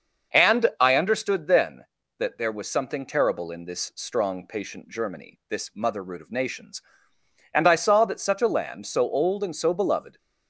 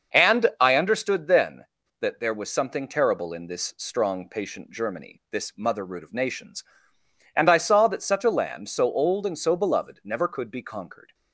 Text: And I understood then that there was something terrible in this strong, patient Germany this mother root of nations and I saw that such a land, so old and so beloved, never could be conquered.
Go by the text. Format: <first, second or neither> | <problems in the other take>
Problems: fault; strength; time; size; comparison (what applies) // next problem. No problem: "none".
second | starts louder than the rest; until 1.4 s; 6.5 dB; also in the second // stops before "never could be conquered"; at 10.1 s